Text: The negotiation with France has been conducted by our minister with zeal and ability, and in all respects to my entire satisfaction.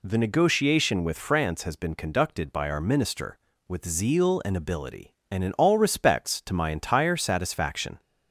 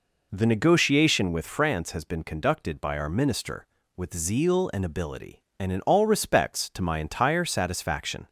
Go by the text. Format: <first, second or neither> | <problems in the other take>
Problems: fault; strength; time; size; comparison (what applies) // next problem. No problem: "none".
first | starts louder than the rest; noticeable; until 1.3 s; 4 dB